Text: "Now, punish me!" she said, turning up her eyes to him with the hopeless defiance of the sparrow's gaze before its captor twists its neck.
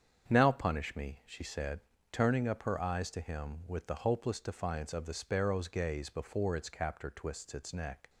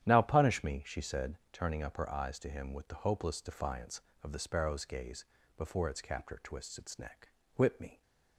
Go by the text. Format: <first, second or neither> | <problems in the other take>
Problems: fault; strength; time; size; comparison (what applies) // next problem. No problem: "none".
first | starts louder than the rest; strong; until 1.1 s; 10.5 dB; strong in the first // pauses between "gaze" and "before"; slight; at 5.2 s; 0.30 s long // goes on to say "Whip me"; slight; from 7.5 s on; 0.46 s long